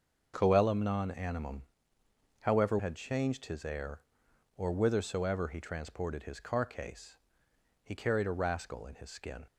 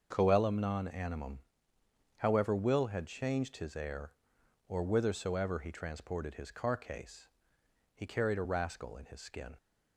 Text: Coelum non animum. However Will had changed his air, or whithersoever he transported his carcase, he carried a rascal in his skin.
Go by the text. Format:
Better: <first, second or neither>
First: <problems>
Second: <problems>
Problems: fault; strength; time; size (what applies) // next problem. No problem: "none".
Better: second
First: starts louder than the rest; until 1.3 s; 6 dB // skips "Will"; at 2.7 s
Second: starts louder than the rest; until 1.1 s; 6.5 dB